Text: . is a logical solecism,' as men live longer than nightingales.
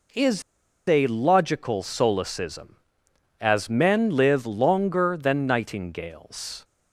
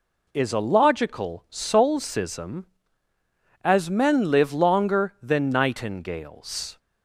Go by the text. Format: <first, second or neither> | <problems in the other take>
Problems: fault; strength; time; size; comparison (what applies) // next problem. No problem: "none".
second | pauses between "is" and "a"; at 0.4 s; 0.45 s long